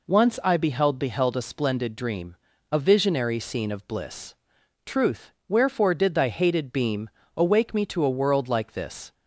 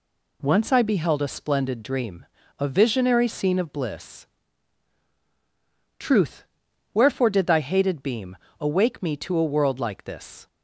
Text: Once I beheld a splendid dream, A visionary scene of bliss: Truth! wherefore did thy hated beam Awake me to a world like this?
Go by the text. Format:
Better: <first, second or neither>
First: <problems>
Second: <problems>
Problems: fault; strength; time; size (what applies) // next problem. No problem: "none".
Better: second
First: says "beheld" twice; at 0.9 s // pauses between "beam" and "Awake"; slight; at 7.0 s; 0.28 s long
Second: pauses between "beam" and "Awake"; slight; at 8.3 s; 0.24 s long